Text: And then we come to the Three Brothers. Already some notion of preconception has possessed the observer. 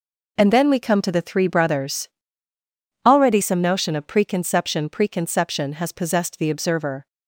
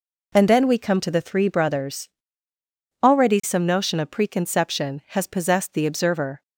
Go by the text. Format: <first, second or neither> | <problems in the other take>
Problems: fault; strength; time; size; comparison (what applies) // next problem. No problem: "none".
second | says "preconception" twice; at 4.8 s